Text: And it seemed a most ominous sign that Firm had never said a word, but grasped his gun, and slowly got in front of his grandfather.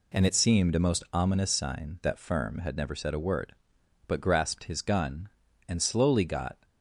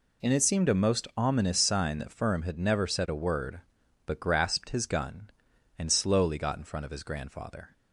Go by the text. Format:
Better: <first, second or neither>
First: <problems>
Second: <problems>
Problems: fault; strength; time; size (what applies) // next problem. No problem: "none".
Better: second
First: stops before "in front of his grandfather"; at 6.6 s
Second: none